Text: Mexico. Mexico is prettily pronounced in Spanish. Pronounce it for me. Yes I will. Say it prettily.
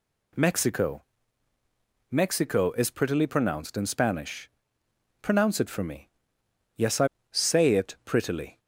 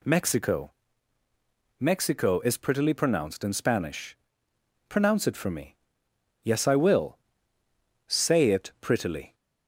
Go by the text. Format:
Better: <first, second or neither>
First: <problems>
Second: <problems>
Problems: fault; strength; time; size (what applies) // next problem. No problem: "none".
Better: second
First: skips "will"; at 7.1 s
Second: none